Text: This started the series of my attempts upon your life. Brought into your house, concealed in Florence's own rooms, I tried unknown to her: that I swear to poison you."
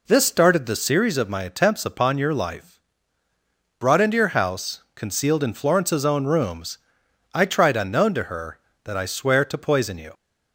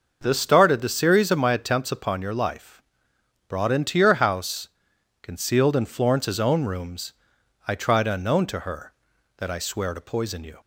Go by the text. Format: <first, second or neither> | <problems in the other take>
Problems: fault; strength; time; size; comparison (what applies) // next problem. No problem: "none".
neither | none